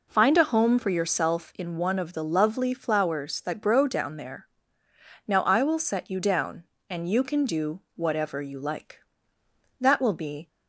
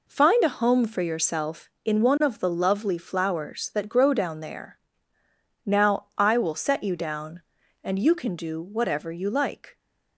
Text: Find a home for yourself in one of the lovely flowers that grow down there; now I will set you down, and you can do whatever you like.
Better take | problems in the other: second | goes on to say "That will be"; noticeable; from 9.8 s on; 0.66 s long

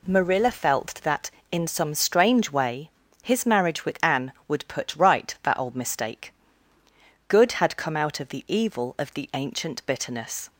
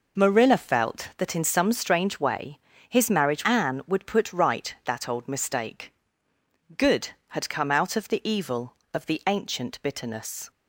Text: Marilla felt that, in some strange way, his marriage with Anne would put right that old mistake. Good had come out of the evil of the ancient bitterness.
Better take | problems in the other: first | skips "with"; at 3.4 s

